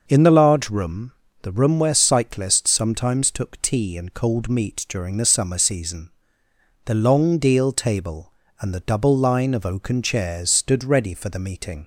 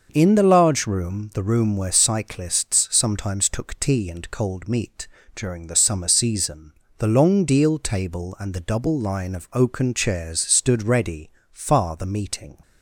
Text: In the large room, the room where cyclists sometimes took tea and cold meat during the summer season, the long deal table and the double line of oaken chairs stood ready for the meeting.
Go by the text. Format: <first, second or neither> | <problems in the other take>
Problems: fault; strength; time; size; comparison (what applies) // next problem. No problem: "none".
first | starts louder than the rest; noticeable; until 1.1 s; 6 dB // pauses between "meat" and "during"; slight; at 5.0 s; 0.30 s long // says "far" for "for"; at 11.5 s